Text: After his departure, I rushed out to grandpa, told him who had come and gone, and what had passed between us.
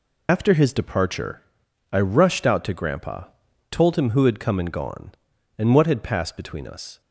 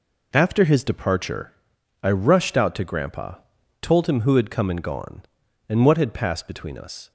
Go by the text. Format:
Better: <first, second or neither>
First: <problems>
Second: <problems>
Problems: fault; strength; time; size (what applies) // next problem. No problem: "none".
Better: second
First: loses the start of "After"; at 0.2 s; 70 ms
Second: none